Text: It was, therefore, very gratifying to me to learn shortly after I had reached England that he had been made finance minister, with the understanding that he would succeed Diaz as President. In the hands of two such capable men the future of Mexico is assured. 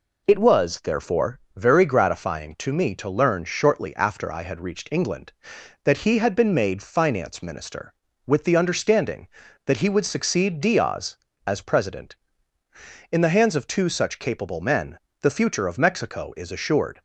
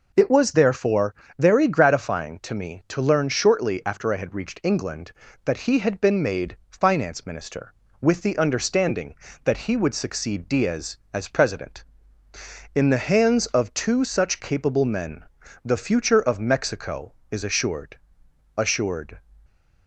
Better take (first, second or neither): first